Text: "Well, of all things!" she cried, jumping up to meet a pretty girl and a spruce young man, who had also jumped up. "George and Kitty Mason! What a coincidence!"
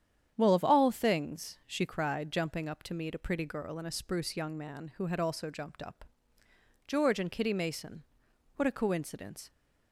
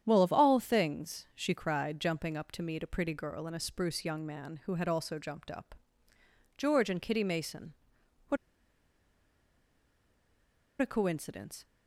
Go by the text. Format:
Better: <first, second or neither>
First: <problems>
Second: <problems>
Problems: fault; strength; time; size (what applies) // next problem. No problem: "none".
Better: first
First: starts louder than the rest; strong; until 1.3 s; 9 dB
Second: starts louder than the rest; strong; until 1.0 s; 9.5 dB // pauses between "What" and "a"; strong; at 8.3 s; 2.4 s long